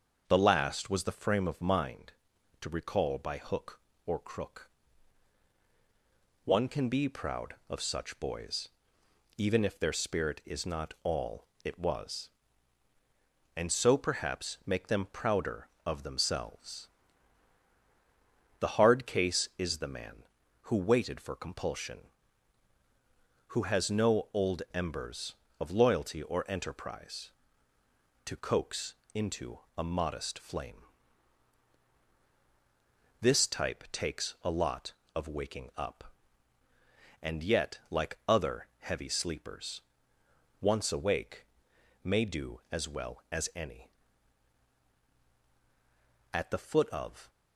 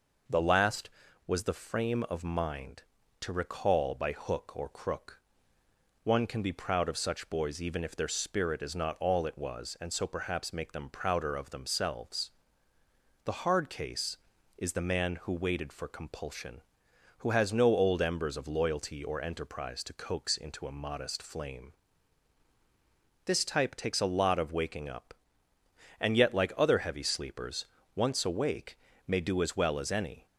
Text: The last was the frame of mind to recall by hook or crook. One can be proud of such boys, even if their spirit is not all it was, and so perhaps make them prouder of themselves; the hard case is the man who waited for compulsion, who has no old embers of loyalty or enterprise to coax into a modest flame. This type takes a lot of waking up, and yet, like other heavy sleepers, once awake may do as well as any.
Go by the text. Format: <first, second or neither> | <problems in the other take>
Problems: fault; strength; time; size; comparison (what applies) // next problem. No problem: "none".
second | starts louder than the rest; until 1.3 s; 6.5 dB // pauses between "all" and "it"; slight; at 11.4 s; 0.18 s long // pauses between "coax" and "into"; slight; at 28.9 s; 0.18 s long // pauses between "into" and "a"; slight; at 29.5 s; 0.18 s long // pauses between "awake" and "may"; noticeable; at 41.4 s; 0.58 s long; slight in the second // goes on to say "At the foot of"; noticeable; from 46.3 s on; 0.96 s long